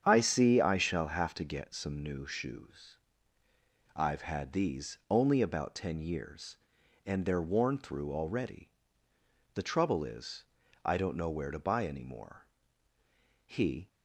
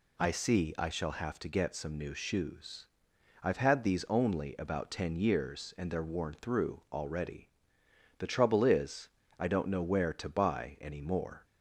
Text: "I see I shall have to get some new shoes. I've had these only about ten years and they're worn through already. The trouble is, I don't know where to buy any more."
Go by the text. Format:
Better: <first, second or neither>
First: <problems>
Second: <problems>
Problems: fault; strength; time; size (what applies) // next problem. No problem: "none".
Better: second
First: starts louder than the rest; strong; until 1.0 s; 8 dB // goes on to say "He"; slight; from 13.4 s on; 0.42 s long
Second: none